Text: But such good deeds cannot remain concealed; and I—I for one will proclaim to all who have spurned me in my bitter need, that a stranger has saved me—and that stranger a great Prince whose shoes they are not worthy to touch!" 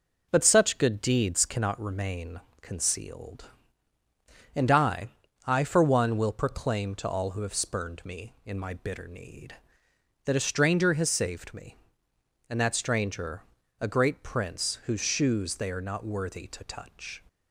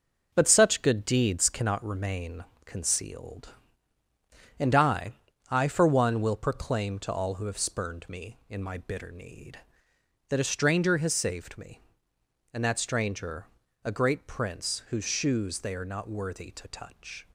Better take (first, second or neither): first